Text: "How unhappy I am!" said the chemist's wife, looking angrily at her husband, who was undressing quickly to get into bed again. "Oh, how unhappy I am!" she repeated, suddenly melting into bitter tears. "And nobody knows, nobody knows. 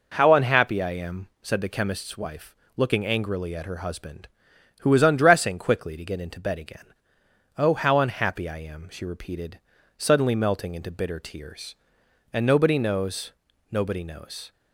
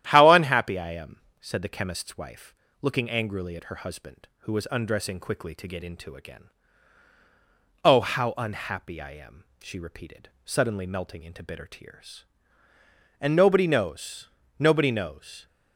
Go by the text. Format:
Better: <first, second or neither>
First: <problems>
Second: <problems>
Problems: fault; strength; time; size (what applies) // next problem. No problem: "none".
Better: first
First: none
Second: starts louder than the rest; strong; until 1.1 s; 12 dB // skips "bed"; at 6.1 s